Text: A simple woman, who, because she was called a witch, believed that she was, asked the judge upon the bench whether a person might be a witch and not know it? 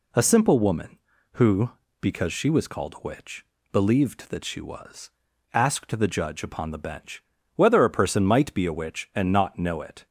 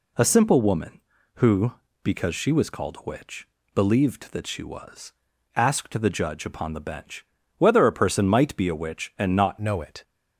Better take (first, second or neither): first